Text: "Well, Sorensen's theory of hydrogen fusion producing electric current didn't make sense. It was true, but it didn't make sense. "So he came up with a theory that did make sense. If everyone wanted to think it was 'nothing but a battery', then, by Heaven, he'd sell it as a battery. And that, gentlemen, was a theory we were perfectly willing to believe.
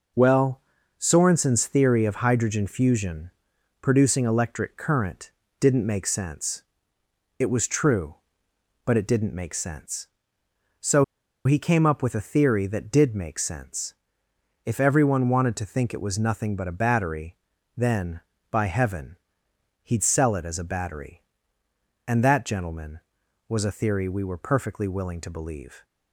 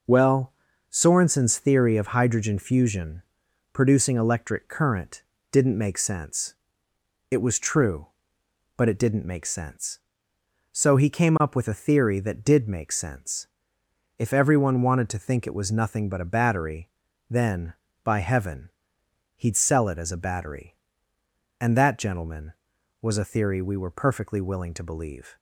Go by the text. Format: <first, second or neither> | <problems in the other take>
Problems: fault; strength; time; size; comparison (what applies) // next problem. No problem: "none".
second | pauses between "fusion" and "producing"; noticeable; at 3.3 s; 0.50 s long; noticeable in the second // pauses between "current" and "didn't"; slight; at 5.3 s; 0.28 s long; slight in the second // pauses between "So" and "he"; at 11.0 s; 0.41 s long